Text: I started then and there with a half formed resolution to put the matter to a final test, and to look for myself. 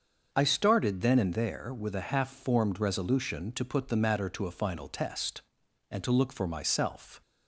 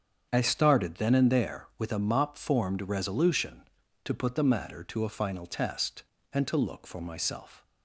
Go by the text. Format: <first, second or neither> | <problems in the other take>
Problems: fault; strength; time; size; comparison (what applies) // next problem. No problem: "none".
first | starts louder than the rest; strong; until 1.3 s; 7.5 dB; also in the first // says "mop" for "half"; at 1.9 s